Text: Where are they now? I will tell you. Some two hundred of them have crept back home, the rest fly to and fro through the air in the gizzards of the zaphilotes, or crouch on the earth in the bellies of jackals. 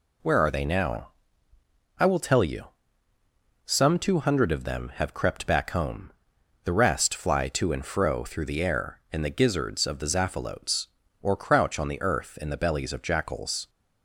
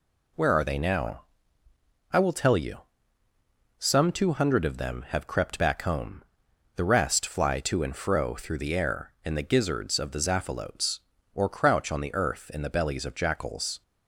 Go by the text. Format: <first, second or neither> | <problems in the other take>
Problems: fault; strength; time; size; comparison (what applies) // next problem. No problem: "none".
neither | none